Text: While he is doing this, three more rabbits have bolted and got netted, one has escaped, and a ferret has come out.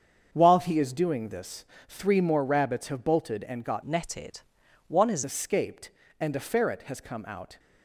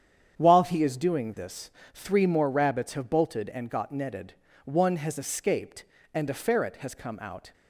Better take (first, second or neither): second